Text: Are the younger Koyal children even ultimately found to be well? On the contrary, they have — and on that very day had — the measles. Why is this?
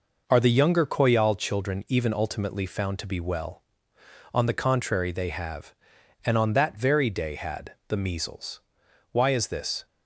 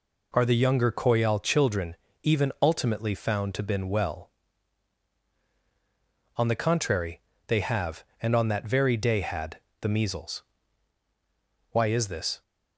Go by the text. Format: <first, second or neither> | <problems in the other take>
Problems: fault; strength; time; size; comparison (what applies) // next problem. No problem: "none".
first | pauses between "children" and "even"; slight; at 1.9 s; 0.28 s long // says "been" for "be"; at 3.6 s